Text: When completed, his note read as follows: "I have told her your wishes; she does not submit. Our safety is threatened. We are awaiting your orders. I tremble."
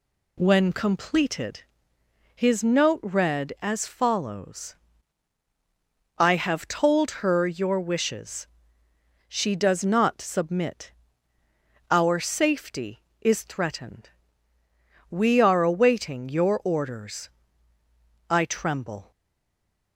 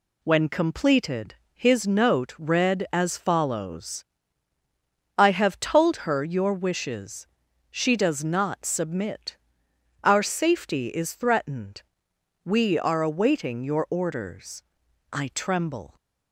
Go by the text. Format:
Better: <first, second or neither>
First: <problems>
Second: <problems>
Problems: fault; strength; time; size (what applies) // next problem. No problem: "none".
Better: second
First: stays silent after the last word; slight; from 19.1 s on; 0.8 s long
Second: none